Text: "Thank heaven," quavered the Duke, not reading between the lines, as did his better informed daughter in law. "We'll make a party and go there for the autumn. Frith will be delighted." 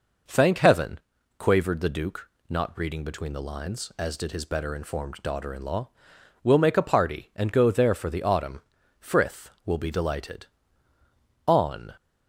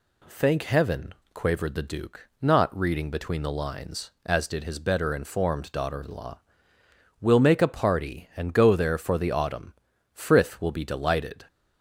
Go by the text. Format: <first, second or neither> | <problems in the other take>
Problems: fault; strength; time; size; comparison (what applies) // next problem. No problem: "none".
second | goes on to say "On"; slight; from 11.4 s on; 0.48 s long